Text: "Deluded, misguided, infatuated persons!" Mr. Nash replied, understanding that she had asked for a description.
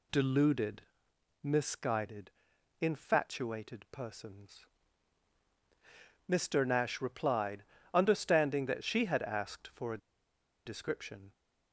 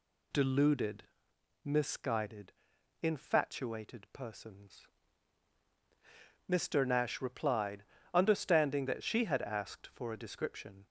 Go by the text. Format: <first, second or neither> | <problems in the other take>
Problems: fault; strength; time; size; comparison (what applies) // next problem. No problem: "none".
second | pauses between "a" and "description"; noticeable; at 9.9 s; 0.67 s long